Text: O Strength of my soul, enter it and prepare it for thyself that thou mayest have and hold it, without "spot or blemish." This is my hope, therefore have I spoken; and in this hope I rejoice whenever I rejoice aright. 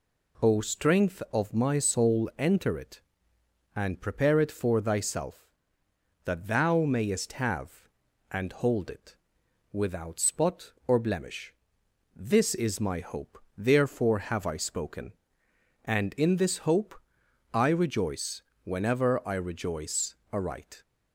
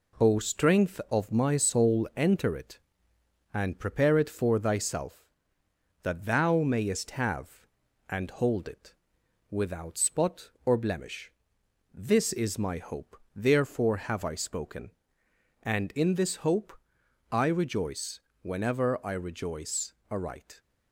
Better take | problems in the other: first | gets quieter; noticeable; throughout; 5 dB // pauses between "hope" and "I"; noticeable; at 16.7 s; 0.60 s long; noticeable in the first // pauses between "rejoice" and "whenever"; slight; at 18.2 s; 0.22 s long; slight in the first // pauses between "rejoice" and "aright"; slight; at 19.9 s; 0.18 s long; slight in the first

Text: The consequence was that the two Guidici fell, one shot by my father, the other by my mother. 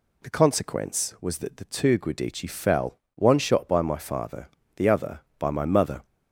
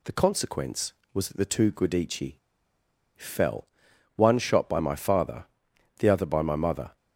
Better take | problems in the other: first | pauses between "Guidici" and "fell"; noticeable; at 2.3 s; 0.79 s long

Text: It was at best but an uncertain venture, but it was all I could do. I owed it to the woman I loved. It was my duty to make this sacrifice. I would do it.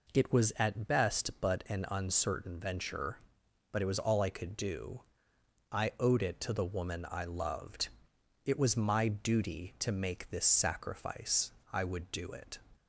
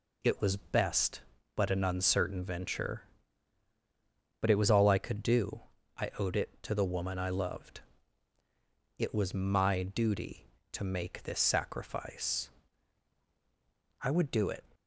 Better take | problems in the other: first | skips "at"; at 0.5 s

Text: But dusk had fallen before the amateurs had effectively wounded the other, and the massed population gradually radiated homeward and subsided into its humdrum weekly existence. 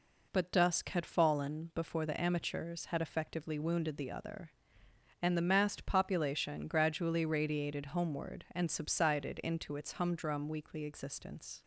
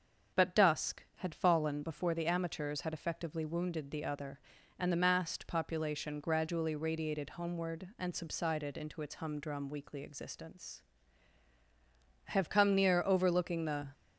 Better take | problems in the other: first | starts louder than the rest; strong; until 1.4 s; 7 dB // goes on to say "I have come near overlooking the"; from 12.2 s on; 1.6 s long

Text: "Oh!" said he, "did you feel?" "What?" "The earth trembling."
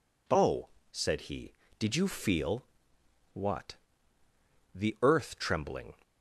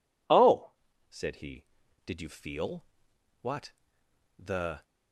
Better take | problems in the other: first | stops before "earth trembling"; at 4.8 s

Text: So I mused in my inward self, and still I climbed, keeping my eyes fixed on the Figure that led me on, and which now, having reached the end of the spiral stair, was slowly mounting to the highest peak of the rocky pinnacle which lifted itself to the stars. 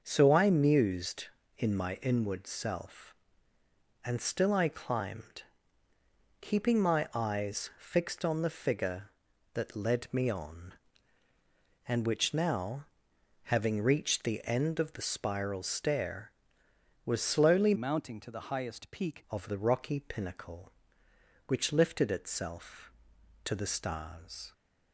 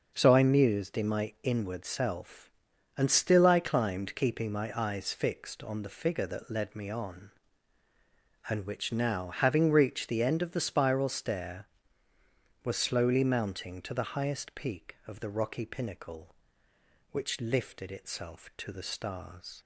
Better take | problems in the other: second | starts louder than the rest; until 1.0 s; 6.5 dB // changes voice from "mounting" to "peak"; from 17.7 to 19.2 s; 1.5 s long

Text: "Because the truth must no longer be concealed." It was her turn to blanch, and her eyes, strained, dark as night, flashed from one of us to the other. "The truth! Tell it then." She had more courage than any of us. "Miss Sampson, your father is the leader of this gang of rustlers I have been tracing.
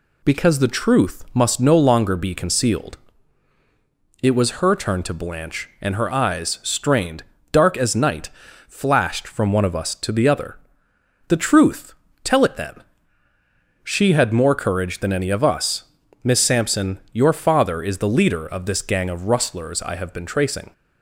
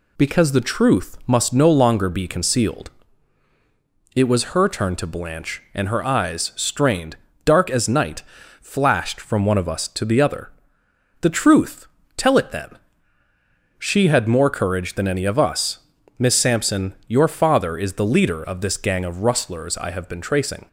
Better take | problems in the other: neither | none

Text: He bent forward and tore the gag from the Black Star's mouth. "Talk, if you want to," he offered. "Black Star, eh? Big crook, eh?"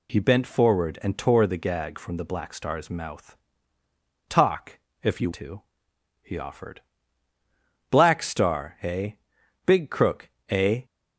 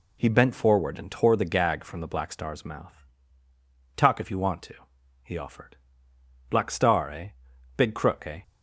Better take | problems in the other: second | skips "want"; at 5.3 s

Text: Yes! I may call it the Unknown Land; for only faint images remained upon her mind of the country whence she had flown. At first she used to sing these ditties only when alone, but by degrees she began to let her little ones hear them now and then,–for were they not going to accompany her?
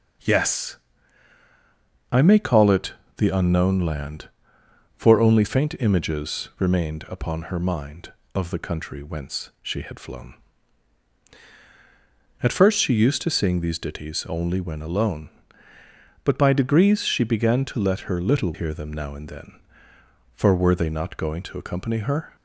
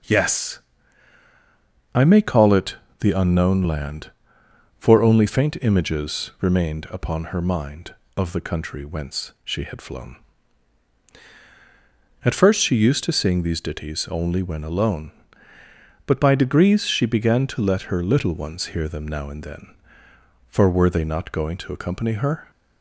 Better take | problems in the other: second | pauses between "it" and "the"; slight; at 2.9 s; 0.24 s long; slight in the second // skips "ones"; at 18.5 s

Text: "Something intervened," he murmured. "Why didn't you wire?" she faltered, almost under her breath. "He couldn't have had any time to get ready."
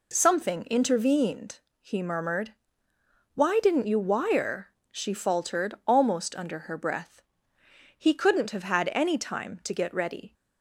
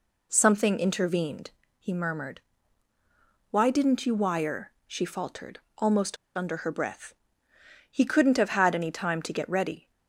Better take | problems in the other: first | pauses between "almost" and "under"; slight; at 6.1 s; 0.22 s long

